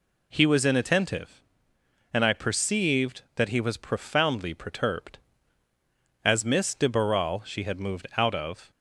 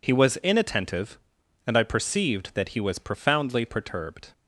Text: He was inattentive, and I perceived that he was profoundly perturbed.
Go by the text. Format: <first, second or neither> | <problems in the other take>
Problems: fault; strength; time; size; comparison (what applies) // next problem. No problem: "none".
second | goes on to say "As Miss de Barral she had moved out of"; strong; from 6.2 s on; 2.4 s long